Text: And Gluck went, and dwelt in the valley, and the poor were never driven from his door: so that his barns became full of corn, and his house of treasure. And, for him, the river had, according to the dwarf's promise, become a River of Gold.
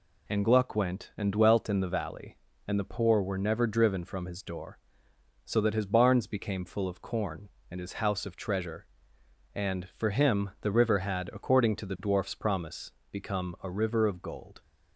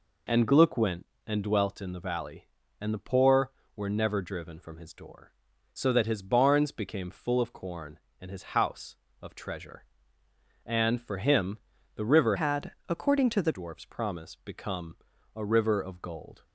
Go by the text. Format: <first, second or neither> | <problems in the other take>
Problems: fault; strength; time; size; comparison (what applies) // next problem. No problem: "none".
first | changes voice from "had" to "the"; from 12.3 to 13.5 s; 1.2 s long // pauses between "become" and "a"; at 14.9 s; 0.40 s long